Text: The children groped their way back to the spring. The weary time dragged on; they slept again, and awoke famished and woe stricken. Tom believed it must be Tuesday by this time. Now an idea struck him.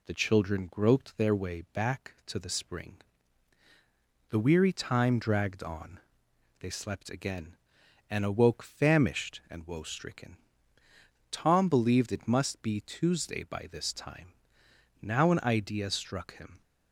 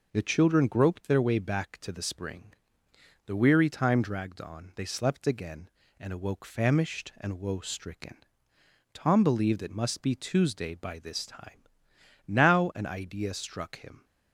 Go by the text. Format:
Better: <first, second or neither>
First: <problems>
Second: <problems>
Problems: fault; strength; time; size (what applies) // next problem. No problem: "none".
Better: neither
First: none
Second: none